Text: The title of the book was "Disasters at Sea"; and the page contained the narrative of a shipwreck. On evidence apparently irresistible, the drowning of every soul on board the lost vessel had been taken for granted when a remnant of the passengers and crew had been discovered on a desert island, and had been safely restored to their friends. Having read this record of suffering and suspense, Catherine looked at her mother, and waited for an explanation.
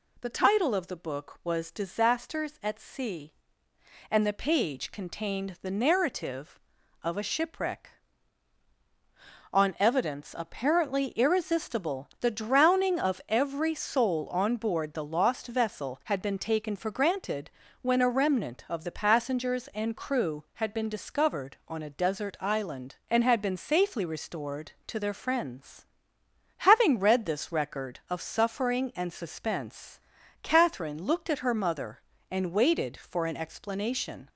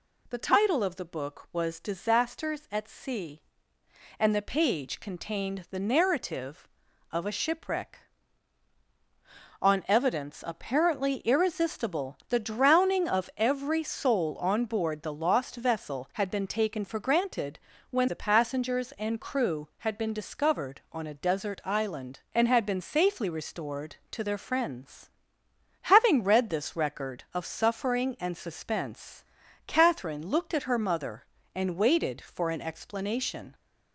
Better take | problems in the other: first | pauses between "granted" and "when"; slight; at 17.5 s; 0.34 s long; slight in the first // skips "a remnant of"; at 18.0 s

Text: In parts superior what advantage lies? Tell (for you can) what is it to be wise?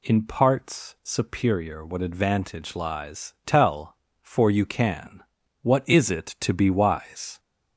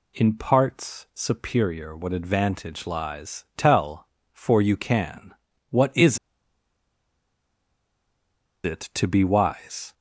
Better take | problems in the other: first | pauses between "is" and "it"; strong; at 6.1 s; 2.4 s long

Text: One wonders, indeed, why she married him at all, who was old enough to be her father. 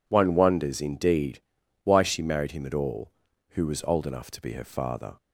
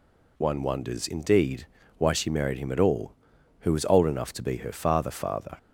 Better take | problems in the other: first | says "father" twice; at 5.1 s

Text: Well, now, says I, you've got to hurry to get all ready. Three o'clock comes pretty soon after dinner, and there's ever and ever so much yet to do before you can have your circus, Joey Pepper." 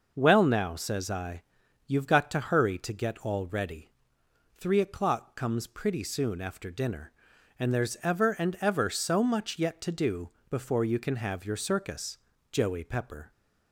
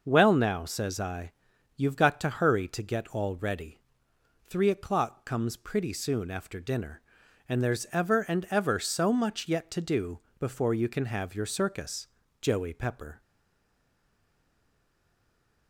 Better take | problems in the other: first | pauses between "do" and "before"; slight; at 10.1 s; 0.20 s long; slight in the first // stays silent after the last word; from 13.2 s on; 2.4 s long

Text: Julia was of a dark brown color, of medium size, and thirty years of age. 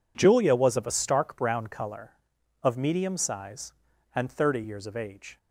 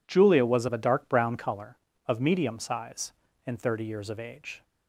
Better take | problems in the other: second | says "stark" for "dark"; at 0.8 s

